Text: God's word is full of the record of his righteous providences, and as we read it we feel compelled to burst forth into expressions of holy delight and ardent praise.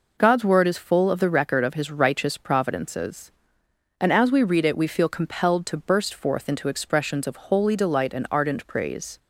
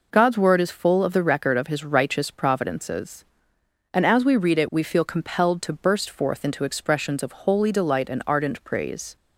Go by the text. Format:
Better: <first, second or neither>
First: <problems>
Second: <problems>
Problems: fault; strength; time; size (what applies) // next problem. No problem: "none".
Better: neither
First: none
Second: none